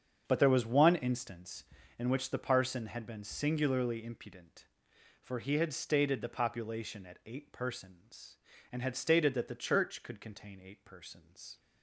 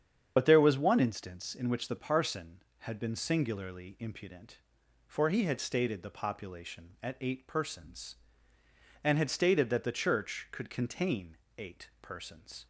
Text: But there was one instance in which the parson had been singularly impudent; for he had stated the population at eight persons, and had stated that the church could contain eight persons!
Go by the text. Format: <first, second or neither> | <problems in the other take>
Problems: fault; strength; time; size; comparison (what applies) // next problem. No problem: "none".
first | loses the start of "But"; at 0.3 s; 45 ms // starts louder than the rest; strong; until 1.3 s; 7.5 dB; strong in the first // pauses between "contain" and "eight"; slight; at 11.3 s; 0.22 s long